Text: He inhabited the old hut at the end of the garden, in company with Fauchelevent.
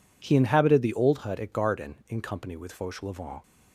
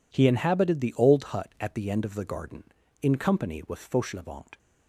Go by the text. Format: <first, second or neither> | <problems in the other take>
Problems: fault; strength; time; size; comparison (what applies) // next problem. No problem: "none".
second | skips "the end of the"; at 1.5 s